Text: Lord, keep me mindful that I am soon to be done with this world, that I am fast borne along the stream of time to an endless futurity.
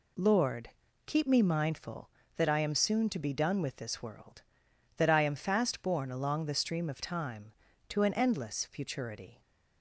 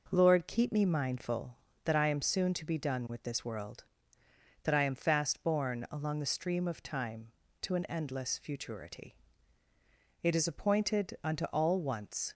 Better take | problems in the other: first | goes on to say "It is appointed unto all once"; strong; from 10.2 s on; 2.1 s long

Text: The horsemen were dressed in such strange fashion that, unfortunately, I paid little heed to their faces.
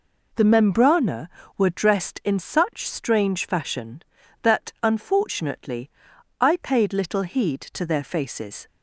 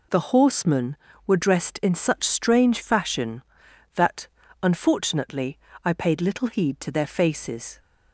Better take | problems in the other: second | says "membrana" for "horsemen"; at 0.4 s

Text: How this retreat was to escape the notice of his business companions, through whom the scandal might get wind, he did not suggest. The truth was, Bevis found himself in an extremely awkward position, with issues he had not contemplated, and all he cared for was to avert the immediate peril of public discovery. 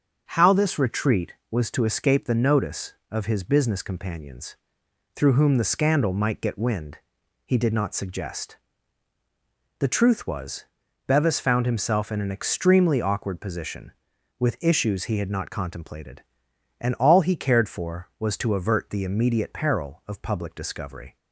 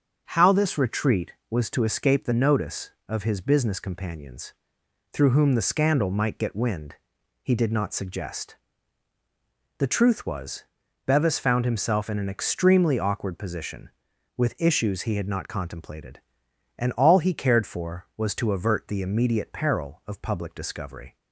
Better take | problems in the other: neither | starts louder than the rest; the same in both

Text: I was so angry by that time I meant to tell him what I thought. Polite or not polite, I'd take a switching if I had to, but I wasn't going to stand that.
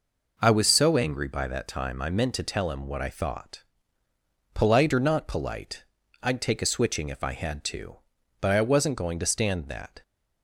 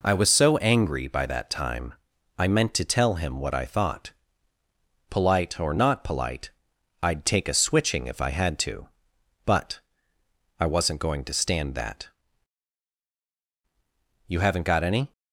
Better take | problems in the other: first | pauses between "time" and "I"; at 1.9 s; 0.42 s long // pauses between "but" and "I"; noticeable; at 9.7 s; 0.78 s long // goes on to say "You haven't got any"; noticeable; from 14.2 s on; 0.84 s long

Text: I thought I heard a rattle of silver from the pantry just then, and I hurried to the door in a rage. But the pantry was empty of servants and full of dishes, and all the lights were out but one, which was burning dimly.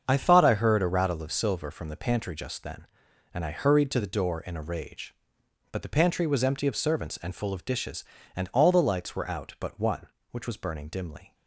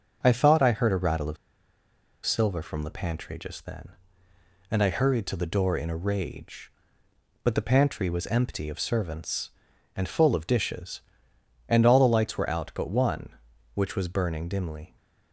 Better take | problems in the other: first | starts louder than the rest; until 1.2 s; 6.5 dB; also in the first // pauses between "of" and "silver"; noticeable; at 1.3 s; 0.89 s long

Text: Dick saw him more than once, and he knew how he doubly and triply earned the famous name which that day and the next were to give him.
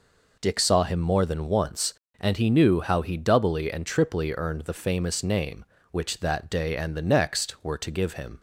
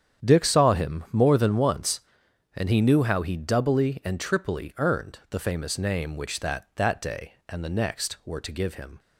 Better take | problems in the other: first | starts louder than the rest; strong; until 1.3 s; 9 dB // says "that" twice; at 6.7 s

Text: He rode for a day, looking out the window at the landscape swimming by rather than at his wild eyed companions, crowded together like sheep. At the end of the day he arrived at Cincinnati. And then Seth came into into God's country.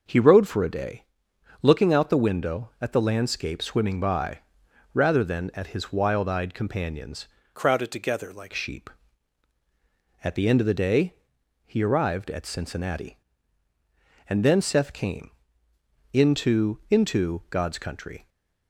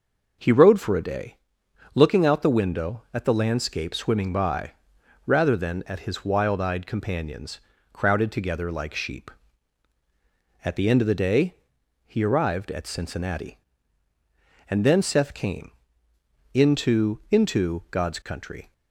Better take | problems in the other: second | pauses between "by" and "rather"; noticeable; at 4.3 s; 0.54 s long; noticeable in the second // changes voice from "crowded" to "like"; from 7.5 to 8.5 s; 1.0 s long // pauses between "day" and "he"; noticeable; at 11.1 s; 0.50 s long; noticeable in the second // pauses between "came" and "into"; noticeable; at 15.3 s; 0.82 s long; noticeable in the second

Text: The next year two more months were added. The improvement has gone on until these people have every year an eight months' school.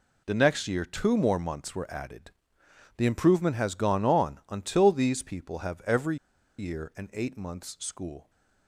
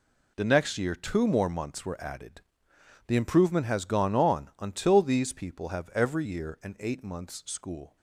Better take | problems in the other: second | pauses between "every" and "year"; at 6.1 s; 0.43 s long

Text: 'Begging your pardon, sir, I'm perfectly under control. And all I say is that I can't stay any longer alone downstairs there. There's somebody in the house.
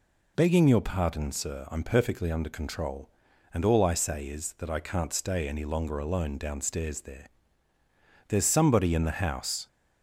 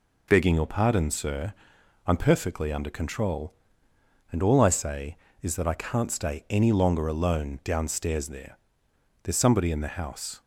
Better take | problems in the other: neither | none

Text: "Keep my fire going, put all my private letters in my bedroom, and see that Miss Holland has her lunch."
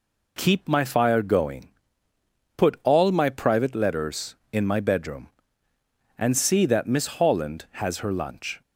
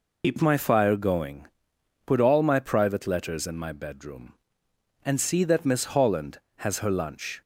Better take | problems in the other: first | loses the start of "Keep"; at 0.2 s; 65 ms

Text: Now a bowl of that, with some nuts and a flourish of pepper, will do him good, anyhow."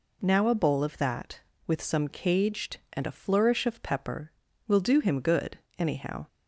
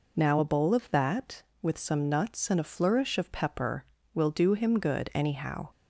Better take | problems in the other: second | says "caged" for "nuts"; at 2.0 s

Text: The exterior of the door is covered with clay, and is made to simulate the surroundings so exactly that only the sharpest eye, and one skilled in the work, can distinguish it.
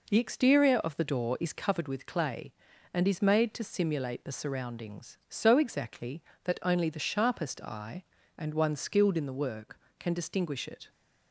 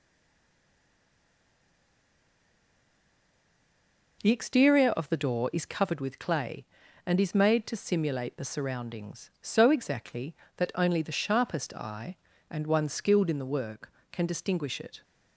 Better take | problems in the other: first | stays silent before the first word; strong; until 4.2 s; 4.2 s long

